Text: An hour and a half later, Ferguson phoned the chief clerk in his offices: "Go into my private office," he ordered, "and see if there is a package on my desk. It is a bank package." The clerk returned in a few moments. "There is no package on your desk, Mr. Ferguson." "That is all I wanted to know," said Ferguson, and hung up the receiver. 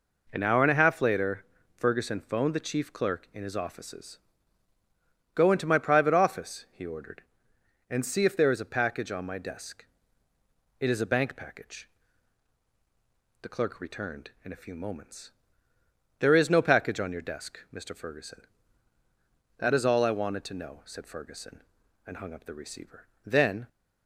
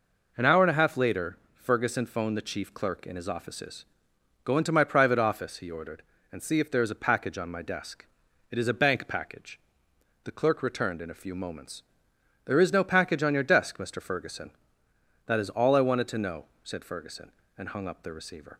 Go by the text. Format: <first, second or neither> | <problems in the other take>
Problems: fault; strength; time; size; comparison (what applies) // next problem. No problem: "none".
second | goes on to say "Then"; slight; from 23.2 s on; 0.44 s long